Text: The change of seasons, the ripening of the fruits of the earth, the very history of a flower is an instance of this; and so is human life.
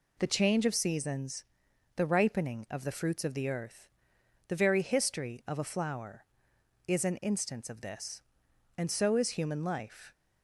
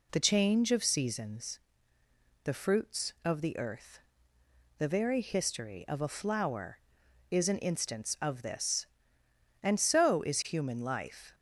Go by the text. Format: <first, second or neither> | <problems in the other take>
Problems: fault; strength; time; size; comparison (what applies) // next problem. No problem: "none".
first | skips "ripening of the"; at 2.5 s